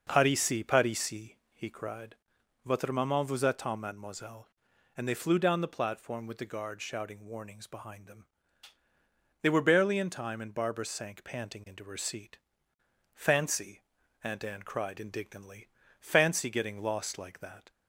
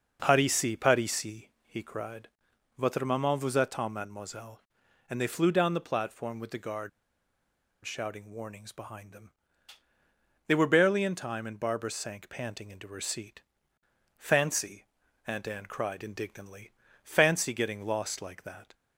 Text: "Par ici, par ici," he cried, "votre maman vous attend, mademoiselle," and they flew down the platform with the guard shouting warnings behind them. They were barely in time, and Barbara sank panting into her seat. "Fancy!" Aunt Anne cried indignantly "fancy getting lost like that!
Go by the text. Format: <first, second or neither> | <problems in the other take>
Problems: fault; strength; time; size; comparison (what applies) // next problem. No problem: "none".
first | pauses between "guard" and "shouting"; noticeable; at 6.8 s; 0.95 s long // pauses between "indignantly" and "fancy"; slight; at 16.7 s; 0.32 s long; slight in the first